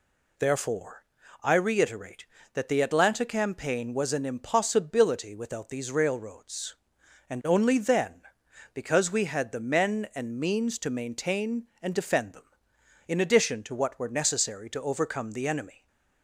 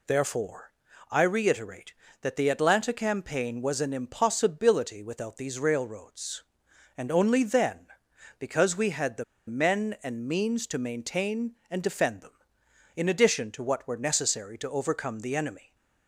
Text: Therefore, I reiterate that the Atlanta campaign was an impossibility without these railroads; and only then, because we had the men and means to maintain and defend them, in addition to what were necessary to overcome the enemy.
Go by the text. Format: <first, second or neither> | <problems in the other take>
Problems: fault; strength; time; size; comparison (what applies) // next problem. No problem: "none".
first | pauses between "the" and "men"; slight; at 9.2 s; 0.24 s long